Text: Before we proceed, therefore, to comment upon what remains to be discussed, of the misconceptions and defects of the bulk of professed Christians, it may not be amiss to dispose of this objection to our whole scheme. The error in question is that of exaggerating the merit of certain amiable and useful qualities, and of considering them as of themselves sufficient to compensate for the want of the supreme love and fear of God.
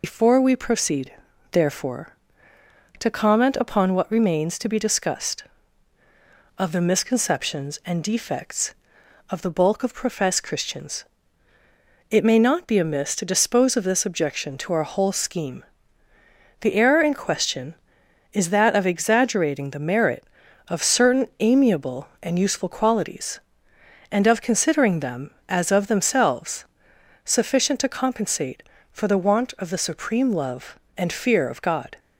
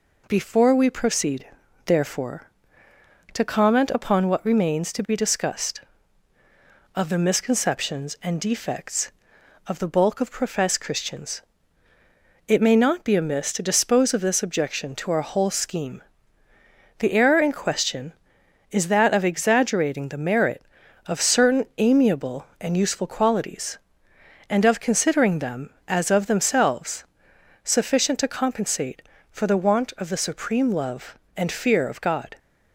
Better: second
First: loses the start of "Before"; at 0.0 s; 125 ms // pauses between "themselves" and "sufficient"; noticeable; at 26.6 s; 0.58 s long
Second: pauses between "themselves" and "sufficient"; noticeable; at 27.0 s; 0.58 s long

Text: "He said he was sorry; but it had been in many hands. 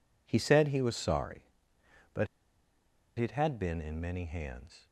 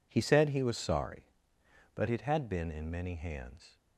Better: second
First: pauses between "but" and "it"; noticeable; at 2.2 s; 0.90 s long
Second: none

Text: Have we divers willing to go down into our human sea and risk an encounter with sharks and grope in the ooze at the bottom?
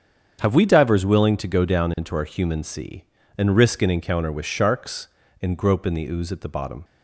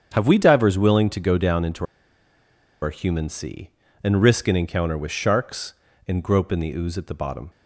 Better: first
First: starts louder than the rest; strong; until 1.4 s; 7.5 dB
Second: starts louder than the rest; strong; until 1.1 s; 7.5 dB // pauses between "into" and "our"; noticeable; at 1.8 s; 0.97 s long

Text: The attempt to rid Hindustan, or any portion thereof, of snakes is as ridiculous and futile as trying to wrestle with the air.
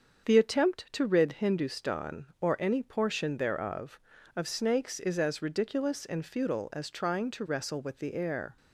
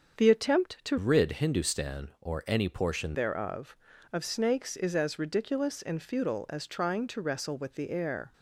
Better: first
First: starts louder than the rest; until 1.3 s; 7 dB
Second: starts louder than the rest; until 1.2 s; 7 dB // changes voice from "rid" to "portion"; from 0.9 to 3.1 s; 2.2 s long

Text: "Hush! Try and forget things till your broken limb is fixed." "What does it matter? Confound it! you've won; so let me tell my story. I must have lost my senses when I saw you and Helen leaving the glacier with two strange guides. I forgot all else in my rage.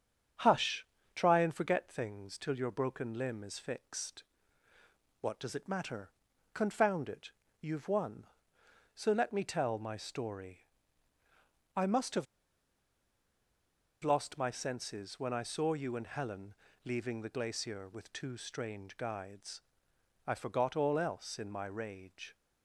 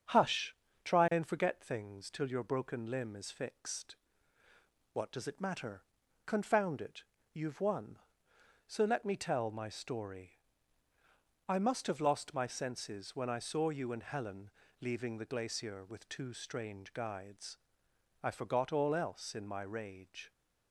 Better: second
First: starts louder than the rest; strong; until 1.6 s; 7.5 dB // pauses between "have" and "lost"; strong; at 12.2 s; 1.7 s long // pauses between "Helen" and "leaving"; slight; at 16.5 s; 0.30 s long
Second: starts louder than the rest; strong; until 1.4 s; 7.5 dB // pauses between "Helen" and "leaving"; slight; at 14.4 s; 0.30 s long

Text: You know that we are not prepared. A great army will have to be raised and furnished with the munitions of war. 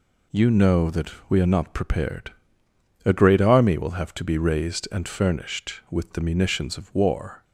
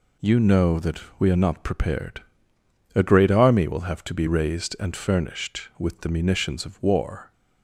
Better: neither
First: pauses between "that" and "we"; slight; at 1.1 s; 0.19 s long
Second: pauses between "that" and "we"; slight; at 0.9 s; 0.20 s long

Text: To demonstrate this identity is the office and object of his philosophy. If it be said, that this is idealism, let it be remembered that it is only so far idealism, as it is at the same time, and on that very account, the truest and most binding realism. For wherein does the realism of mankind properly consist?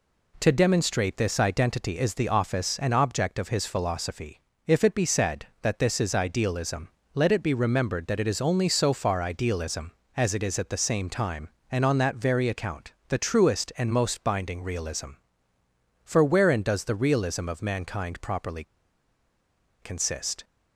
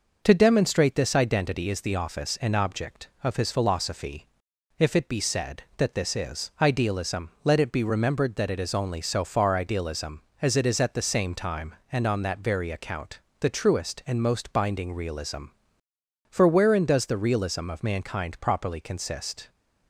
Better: second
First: pauses between "properly" and "consist"; at 18.6 s; 1.1 s long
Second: none

